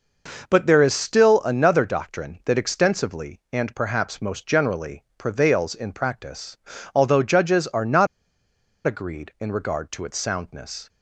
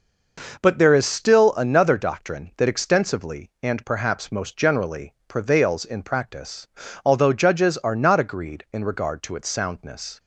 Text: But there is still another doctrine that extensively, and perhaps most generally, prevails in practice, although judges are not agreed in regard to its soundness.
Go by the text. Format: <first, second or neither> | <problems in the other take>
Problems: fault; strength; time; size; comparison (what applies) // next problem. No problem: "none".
second | pauses between "not" and "agreed"; noticeable; at 8.0 s; 0.79 s long